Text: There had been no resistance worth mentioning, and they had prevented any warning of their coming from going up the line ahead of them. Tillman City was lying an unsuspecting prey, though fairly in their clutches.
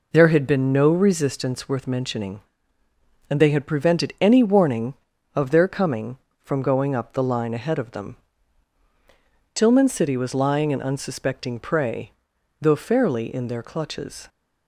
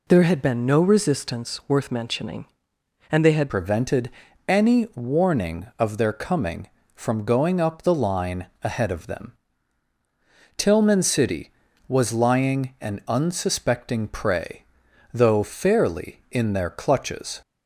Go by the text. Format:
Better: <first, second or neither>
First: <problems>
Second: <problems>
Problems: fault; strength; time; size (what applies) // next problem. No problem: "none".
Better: first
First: none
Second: changes voice at "prevented"; from 3.4 s on; 13.9 s long // pauses between "prevented" and "any"; slight; at 4.0 s; 0.36 s long // pauses between "line" and "ahead"; slight; at 8.4 s; 0.16 s long